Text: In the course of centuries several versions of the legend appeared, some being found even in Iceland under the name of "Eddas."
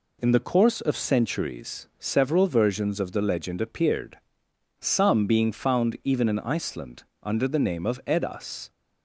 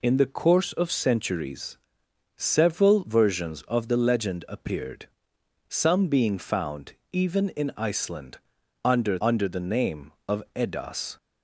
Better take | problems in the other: first | pauses between "centuries" and "several"; noticeable; at 1.7 s; 0.60 s long // pauses between "found" and "even"; slight; at 6.9 s; 0.20 s long // pauses between "Iceland" and "under"; noticeable; at 8.3 s; 0.48 s long; slight in the first // says "under" twice; at 9.2 s

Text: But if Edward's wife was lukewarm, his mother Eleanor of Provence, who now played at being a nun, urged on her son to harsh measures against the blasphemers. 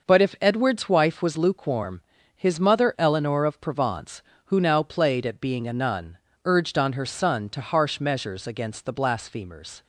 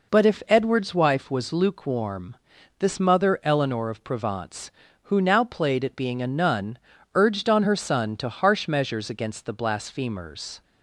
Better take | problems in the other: first | says "this" for "his"; at 2.7 s

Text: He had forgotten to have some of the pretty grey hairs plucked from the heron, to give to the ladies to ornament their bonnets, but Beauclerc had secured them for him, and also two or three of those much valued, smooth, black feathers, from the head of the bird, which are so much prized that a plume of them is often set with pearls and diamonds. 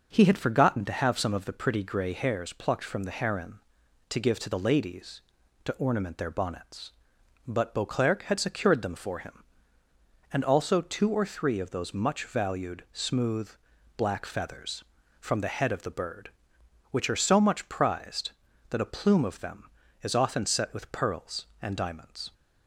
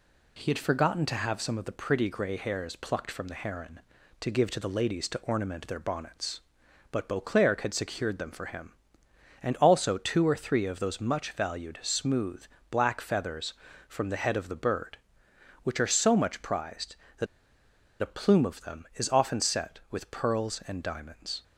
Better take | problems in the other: first | pauses between "that" and "a"; noticeable; at 17.2 s; 0.76 s long

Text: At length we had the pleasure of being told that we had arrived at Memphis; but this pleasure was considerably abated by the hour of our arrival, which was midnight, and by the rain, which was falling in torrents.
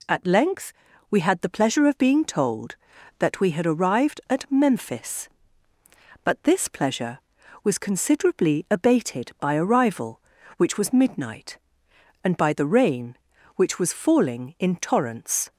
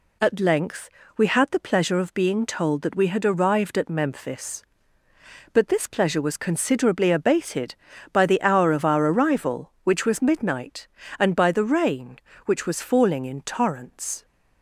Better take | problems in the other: second | pauses between "length" and "we"; at 0.7 s; 0.38 s long; slight in the second // skips "the hour of our"; at 9.5 s

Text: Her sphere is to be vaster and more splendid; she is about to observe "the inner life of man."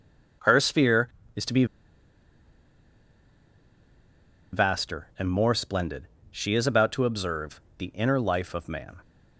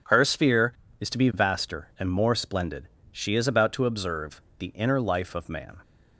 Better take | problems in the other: second | pauses between "be" and "vaster"; strong; at 1.6 s; 2.8 s long // pauses between "observe" and "the"; slight; at 7.5 s; 0.20 s long; slight in the second

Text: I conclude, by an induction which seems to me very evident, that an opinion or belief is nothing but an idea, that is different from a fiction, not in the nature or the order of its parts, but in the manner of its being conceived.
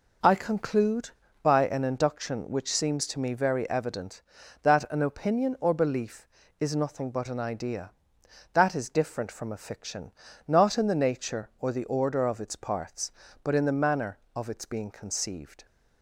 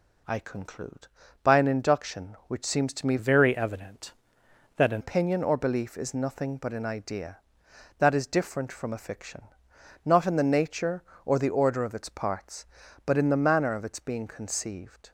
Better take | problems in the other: first | changes voice from "very" to "an"; from 3.1 to 5.0 s; 1.9 s long

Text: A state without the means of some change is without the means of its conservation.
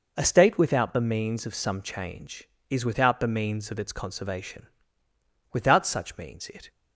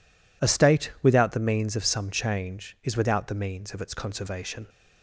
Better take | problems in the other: second | goes on to say "Without such means it"; noticeable; from 5.5 s on; 1.1 s long

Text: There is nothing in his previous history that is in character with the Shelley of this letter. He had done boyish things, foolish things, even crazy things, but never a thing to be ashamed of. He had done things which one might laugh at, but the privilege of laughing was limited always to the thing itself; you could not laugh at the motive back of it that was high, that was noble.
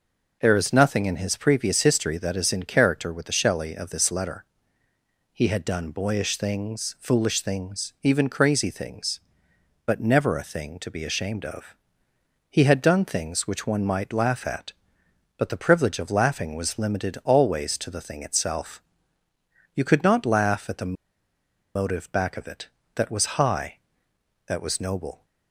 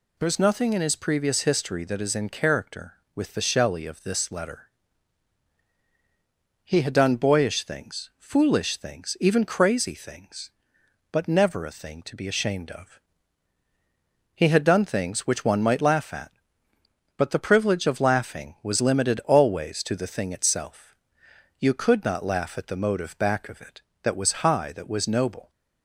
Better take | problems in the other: second | pauses between "the" and "motive"; noticeable; at 20.9 s; 0.82 s long

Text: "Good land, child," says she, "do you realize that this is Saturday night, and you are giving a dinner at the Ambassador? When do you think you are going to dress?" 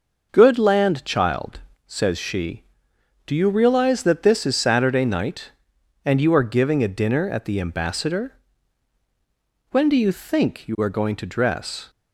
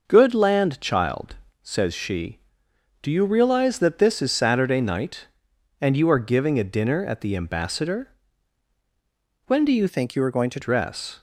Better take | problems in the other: first | changes voice from "think" to "to"; from 9.8 to 10.5 s; 0.7 s long

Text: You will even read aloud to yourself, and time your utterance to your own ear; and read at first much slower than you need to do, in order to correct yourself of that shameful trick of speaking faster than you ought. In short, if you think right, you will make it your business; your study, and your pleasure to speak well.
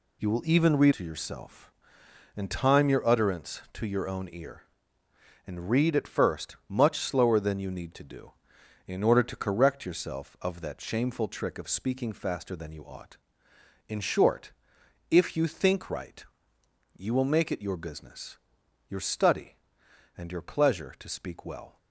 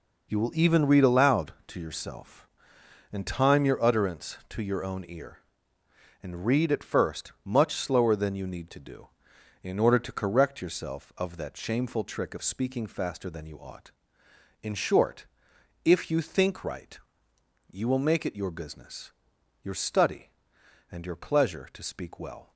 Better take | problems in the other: second | skips "aloud"; at 0.9 s

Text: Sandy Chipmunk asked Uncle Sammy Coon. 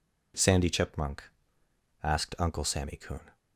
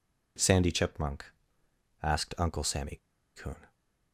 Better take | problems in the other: first | pauses between "Chipmunk" and "asked"; noticeable; at 1.2 s; 0.78 s long; noticeable in the first // pauses between "Sammy" and "Coon"; at 2.9 s; 0.40 s long

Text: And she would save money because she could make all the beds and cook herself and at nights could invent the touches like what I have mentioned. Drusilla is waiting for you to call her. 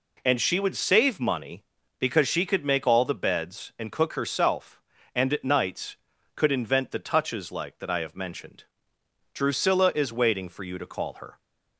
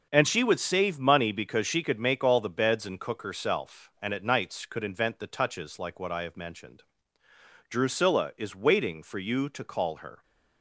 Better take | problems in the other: second | says "that" for "what"; at 7.7 s

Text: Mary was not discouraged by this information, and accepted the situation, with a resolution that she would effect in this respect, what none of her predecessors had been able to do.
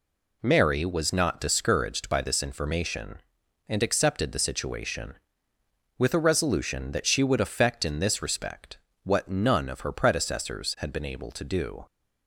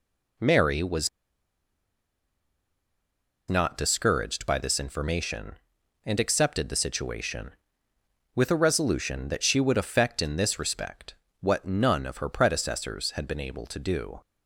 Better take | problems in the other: first | pauses between "was" and "not"; strong; at 1.0 s; 2.3 s long

